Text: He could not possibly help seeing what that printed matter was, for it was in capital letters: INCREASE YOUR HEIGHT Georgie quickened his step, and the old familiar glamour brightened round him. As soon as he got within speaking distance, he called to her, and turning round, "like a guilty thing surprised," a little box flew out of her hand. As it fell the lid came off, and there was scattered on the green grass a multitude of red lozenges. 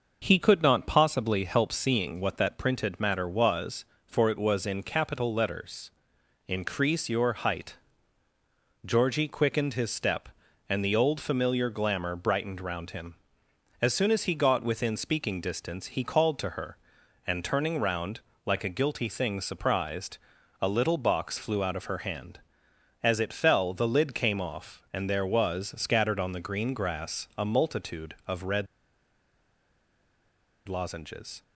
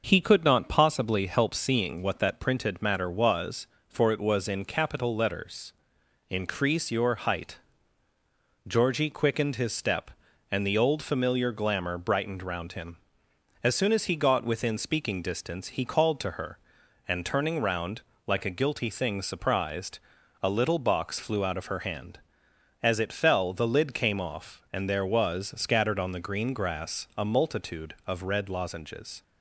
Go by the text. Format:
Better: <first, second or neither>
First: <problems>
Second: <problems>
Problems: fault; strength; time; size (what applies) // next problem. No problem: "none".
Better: second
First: pauses between "HEIGHT" and "Georgie"; at 7.7 s; 1.1 s long // pauses between "red" and "lozenges"; strong; at 28.6 s; 2.0 s long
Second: pauses between "HEIGHT" and "Georgie"; at 7.5 s; 1.1 s long